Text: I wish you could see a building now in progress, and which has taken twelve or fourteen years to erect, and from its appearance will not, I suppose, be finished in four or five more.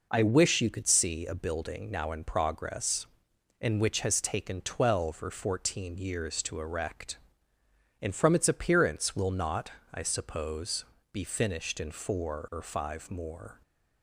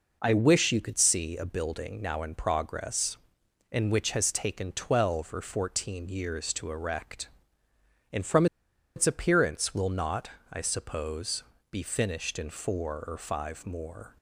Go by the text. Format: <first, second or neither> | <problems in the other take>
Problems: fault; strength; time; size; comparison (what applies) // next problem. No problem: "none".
first | pauses between "from" and "its"; noticeable; at 8.4 s; 0.50 s long